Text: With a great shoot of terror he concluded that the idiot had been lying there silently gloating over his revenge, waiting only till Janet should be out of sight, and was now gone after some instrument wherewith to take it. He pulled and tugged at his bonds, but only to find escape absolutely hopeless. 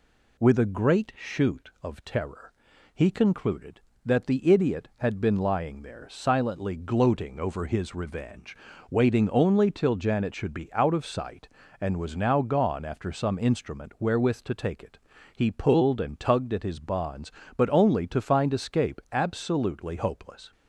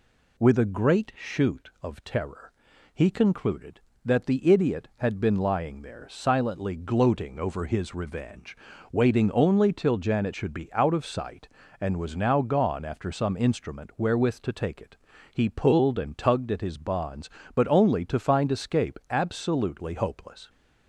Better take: neither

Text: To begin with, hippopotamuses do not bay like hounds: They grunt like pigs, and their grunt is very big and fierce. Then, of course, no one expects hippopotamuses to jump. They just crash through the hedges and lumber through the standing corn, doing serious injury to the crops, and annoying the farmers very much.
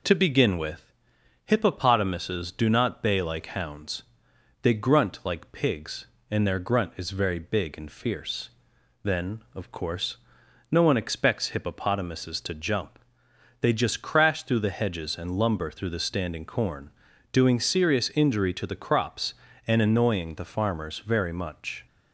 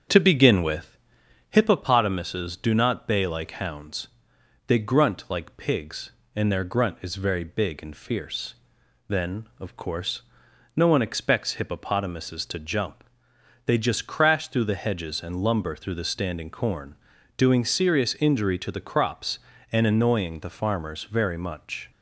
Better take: first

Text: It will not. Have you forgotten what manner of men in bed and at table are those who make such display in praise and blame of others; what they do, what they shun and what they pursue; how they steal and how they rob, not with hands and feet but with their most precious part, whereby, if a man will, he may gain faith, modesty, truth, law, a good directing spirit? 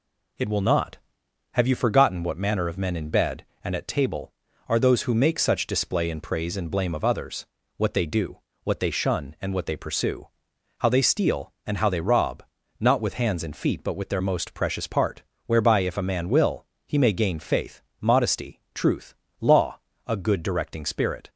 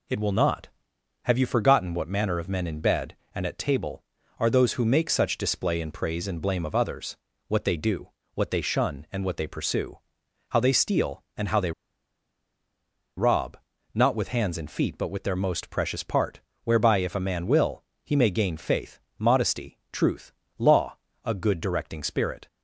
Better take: first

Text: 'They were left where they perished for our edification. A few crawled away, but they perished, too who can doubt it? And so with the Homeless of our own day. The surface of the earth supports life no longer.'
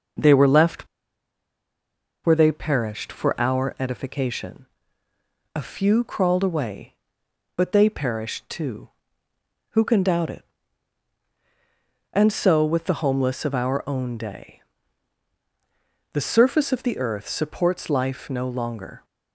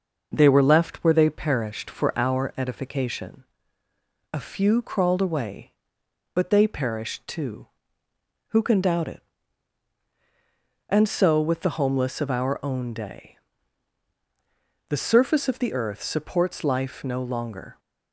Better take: second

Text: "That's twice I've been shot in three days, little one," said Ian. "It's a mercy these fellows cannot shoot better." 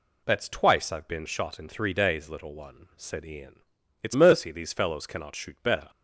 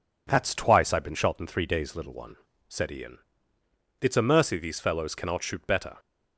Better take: second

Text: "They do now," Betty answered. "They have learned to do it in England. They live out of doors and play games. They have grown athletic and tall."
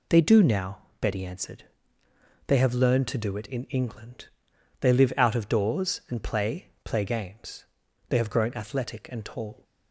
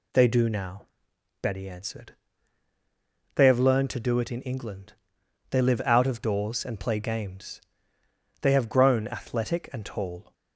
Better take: second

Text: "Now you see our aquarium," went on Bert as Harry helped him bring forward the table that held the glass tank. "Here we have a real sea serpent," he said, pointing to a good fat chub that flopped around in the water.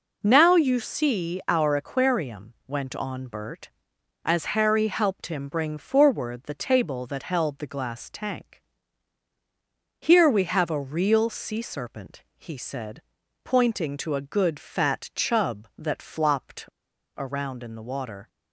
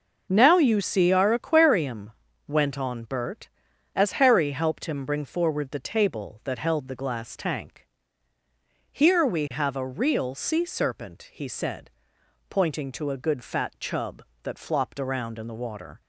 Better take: second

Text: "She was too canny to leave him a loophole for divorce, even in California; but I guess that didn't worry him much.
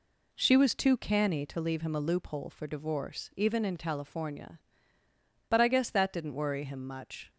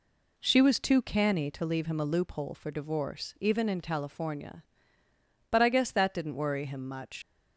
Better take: first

